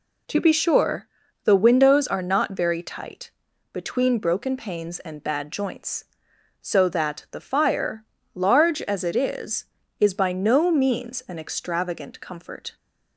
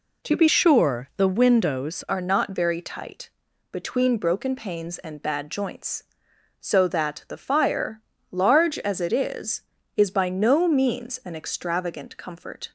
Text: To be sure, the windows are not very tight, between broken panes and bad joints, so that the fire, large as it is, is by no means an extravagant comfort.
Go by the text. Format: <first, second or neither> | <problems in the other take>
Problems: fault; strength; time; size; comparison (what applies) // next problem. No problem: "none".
first | changes voice from "sure" to "windows"; from 0.4 to 2.0 s; 1.6 s long